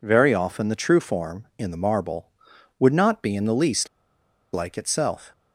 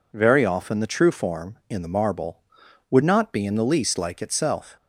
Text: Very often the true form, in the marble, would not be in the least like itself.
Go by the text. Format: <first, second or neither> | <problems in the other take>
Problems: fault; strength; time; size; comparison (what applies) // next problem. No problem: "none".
second | pauses between "least" and "like"; noticeable; at 3.8 s; 0.65 s long